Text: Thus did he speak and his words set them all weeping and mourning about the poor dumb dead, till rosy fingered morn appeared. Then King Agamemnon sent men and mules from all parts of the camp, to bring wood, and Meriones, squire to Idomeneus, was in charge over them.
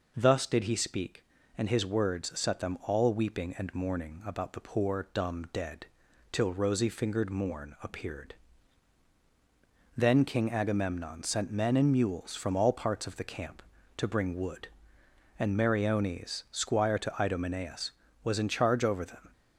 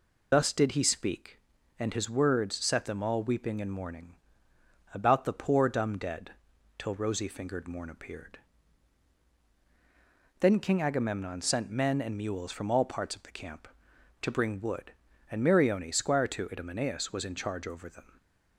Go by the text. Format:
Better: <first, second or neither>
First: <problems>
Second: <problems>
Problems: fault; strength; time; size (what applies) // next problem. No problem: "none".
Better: first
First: none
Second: loses the start of "Thus"; at 0.3 s; 40 ms // pauses between "mourning" and "about"; noticeable; at 4.1 s; 0.80 s long